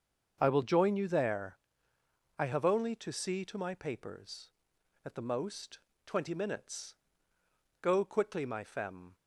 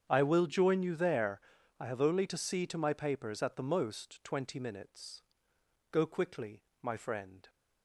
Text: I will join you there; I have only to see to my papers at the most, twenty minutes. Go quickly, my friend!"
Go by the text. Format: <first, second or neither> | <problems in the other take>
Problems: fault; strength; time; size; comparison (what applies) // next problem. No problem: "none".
second | starts louder than the rest; until 1.4 s; 7 dB; strong in the second // says "femme" for "friend"; at 8.6 s